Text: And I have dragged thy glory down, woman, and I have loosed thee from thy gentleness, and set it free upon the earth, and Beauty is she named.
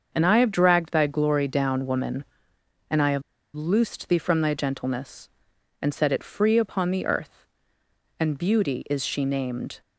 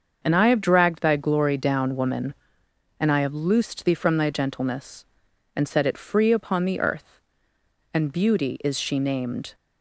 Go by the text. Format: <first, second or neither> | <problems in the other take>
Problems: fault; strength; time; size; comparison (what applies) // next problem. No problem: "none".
second | starts louder than the rest; until 1.1 s; 6.5 dB; also in the second // pauses between "have" and "loosed"; slight; at 3.2 s; 0.34 s long